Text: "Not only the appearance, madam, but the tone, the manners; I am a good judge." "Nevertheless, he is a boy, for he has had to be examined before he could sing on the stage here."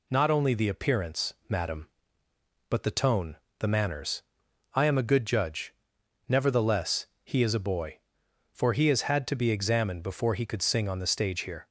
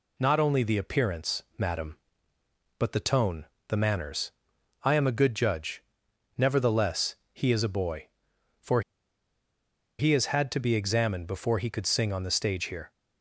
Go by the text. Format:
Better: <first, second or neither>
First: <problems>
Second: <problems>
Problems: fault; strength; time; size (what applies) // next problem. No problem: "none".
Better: first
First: none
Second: pauses between "for" and "he"; at 8.8 s; 1.1 s long